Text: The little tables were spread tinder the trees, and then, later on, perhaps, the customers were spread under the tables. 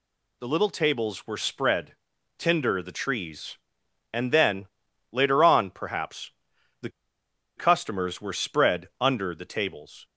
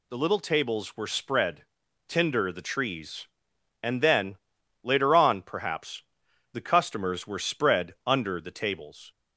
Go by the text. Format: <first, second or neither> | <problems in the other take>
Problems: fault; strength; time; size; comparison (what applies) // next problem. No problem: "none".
second | pauses between "spread" and "tinder"; at 1.9 s; 0.42 s long; also in the second // pauses between "the" and "customers"; noticeable; at 6.8 s; 0.67 s long